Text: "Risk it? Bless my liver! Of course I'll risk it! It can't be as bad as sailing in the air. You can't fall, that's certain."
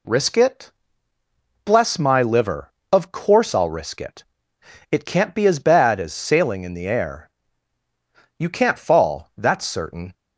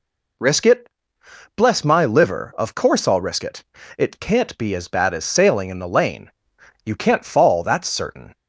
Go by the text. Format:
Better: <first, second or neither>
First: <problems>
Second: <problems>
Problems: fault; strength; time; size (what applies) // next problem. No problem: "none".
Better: first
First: none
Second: says "lane" for "air"; at 5.8 s